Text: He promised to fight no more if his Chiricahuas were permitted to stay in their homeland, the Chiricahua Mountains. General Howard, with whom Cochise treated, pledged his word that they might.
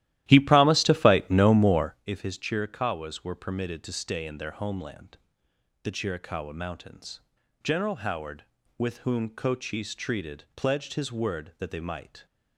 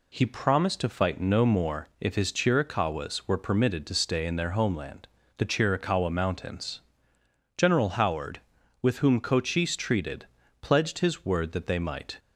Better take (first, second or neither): second